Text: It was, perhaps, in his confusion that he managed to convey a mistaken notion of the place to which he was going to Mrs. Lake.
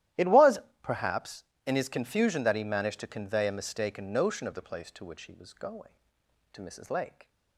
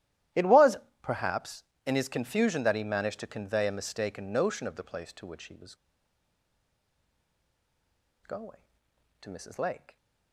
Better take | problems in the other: first | starts louder than the rest; strong; until 1.5 s; 13 dB; strong in the first // pauses between "was" and "going"; strong; at 5.7 s; 2.4 s long

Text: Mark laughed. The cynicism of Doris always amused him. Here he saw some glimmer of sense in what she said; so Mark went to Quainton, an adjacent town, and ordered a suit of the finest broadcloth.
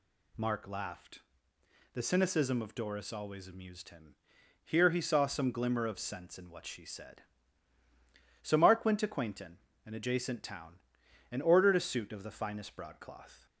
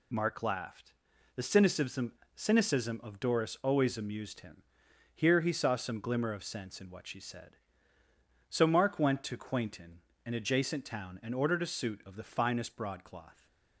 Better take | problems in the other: first | says "cynicism" twice; at 2.3 s

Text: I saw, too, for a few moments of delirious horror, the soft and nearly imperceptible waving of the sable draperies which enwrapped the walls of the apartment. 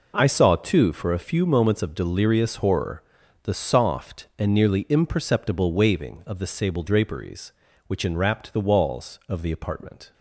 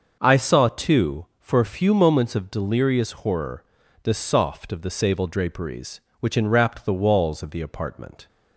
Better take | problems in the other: first | starts louder than the rest; until 1.2 s; 6 dB // skips "and nearly imperceptible waving"; at 4.7 s

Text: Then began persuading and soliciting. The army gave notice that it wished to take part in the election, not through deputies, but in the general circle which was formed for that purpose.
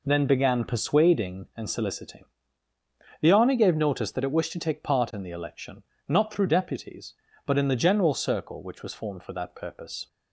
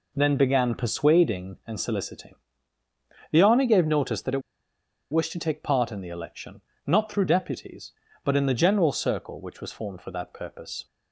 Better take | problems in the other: first | pauses between "it" and "wished"; noticeable; at 4.4 s; 0.70 s long

